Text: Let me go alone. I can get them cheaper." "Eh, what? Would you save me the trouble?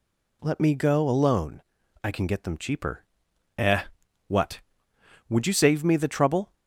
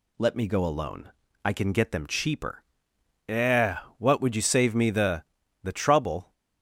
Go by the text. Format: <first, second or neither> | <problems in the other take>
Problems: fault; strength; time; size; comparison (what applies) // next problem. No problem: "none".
first | says "the" twice; at 5.6 s